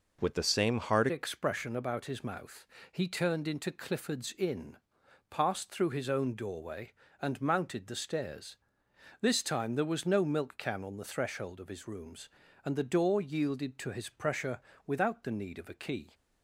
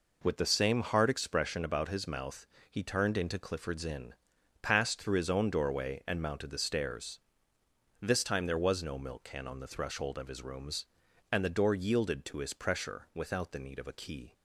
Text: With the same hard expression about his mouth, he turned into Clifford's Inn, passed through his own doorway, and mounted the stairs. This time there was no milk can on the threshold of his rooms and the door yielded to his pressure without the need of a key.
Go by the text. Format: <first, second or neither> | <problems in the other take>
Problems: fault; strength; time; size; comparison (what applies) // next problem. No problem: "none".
second | changes voice at "expression"; from 1.0 s on; 15.1 s long // pauses between "pressure" and "without"; slight; at 14.6 s; 0.26 s long